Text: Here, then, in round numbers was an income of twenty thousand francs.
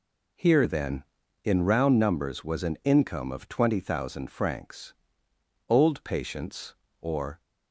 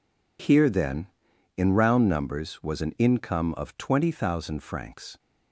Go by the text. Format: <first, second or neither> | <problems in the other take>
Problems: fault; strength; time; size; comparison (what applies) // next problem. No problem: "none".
second | goes on to say "Old patients or"; strong; from 5.6 s on; 1.7 s long